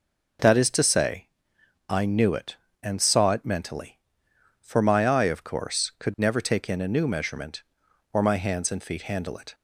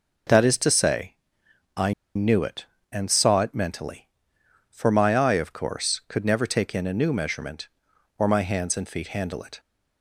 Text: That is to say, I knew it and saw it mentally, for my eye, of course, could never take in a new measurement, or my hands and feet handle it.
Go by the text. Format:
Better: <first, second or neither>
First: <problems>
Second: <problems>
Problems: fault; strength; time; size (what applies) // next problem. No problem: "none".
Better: first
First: none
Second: pauses between "I" and "knew"; slight; at 1.9 s; 0.22 s long